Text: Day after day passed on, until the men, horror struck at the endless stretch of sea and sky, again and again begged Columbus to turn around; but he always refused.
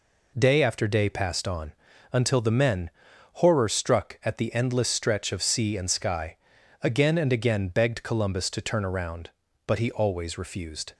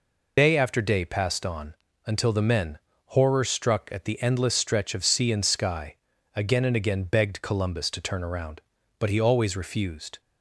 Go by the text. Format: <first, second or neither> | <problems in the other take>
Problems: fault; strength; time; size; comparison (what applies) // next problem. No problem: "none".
first | loses the start of "Day"; at 0.3 s; 95 ms